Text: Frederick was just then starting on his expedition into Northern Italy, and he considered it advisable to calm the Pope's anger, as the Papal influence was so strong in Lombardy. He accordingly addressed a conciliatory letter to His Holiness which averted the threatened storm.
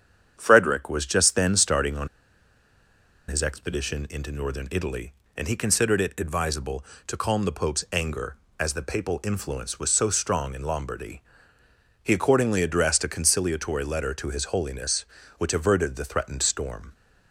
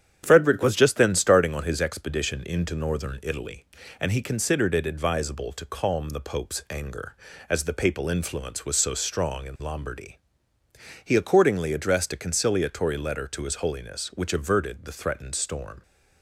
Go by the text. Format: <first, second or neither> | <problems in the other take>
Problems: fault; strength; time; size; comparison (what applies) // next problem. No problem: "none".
second | starts louder than the rest; strong; until 1.3 s; 8 dB; strong in the second // pauses between "on" and "his"; at 2.0 s; 1.2 s long